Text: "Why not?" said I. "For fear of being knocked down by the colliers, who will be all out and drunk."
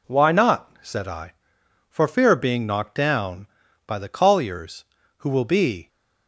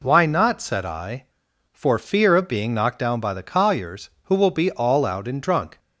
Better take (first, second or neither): second